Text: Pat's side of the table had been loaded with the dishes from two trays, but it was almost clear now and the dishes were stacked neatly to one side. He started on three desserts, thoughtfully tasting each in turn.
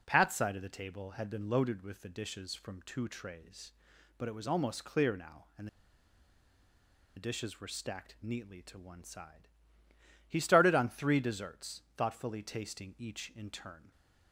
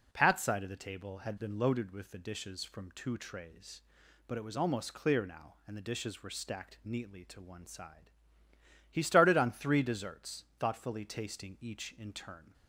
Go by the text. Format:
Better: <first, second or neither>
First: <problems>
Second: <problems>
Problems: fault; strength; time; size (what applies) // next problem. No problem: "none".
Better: second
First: pauses between "and" and "the"; strong; at 5.6 s; 1.4 s long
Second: none